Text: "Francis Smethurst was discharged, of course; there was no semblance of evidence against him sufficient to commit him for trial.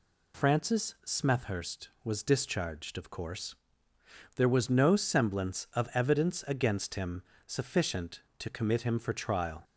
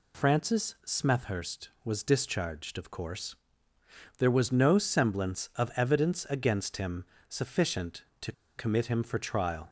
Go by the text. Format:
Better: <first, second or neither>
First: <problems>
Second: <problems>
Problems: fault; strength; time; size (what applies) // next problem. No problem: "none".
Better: first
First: pauses between "him" and "sufficient"; slight; at 7.2 s; 0.24 s long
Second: pauses between "him" and "sufficient"; slight; at 7.0 s; 0.24 s long // pauses between "to" and "commit"; slight; at 8.3 s; 0.25 s long